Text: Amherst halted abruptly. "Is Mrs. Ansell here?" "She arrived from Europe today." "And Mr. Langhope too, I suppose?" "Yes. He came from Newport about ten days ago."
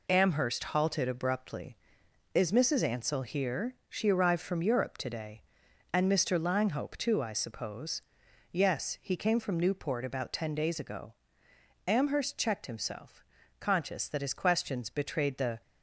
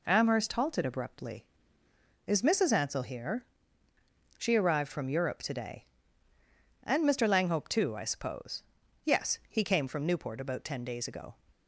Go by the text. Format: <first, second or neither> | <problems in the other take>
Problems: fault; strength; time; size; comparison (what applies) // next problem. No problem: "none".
second | goes on to say "Amherst checked himself conscious that his questions betrayed the"; strong; from 11.8 s on; 3.7 s long